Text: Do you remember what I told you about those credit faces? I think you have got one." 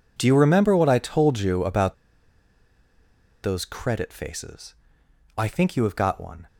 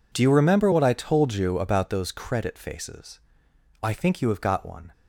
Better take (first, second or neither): second